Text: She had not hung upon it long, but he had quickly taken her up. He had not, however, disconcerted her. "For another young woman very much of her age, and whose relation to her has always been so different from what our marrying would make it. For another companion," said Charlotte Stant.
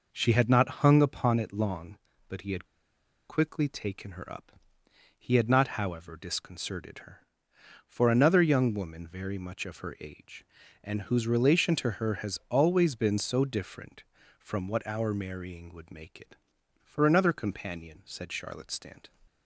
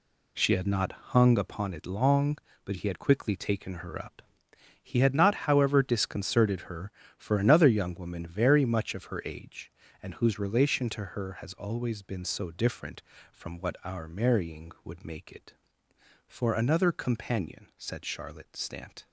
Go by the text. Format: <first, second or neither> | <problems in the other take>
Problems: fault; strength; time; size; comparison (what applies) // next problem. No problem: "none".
second | pauses between "had" and "quickly"; noticeable; at 2.6 s; 0.62 s long